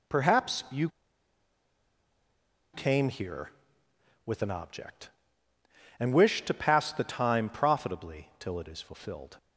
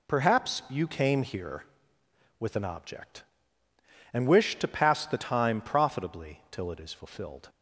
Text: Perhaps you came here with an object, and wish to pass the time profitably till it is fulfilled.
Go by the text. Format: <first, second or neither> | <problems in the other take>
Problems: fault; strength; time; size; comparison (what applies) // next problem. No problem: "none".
second | pauses between "you" and "came"; strong; at 0.8 s; 1.8 s long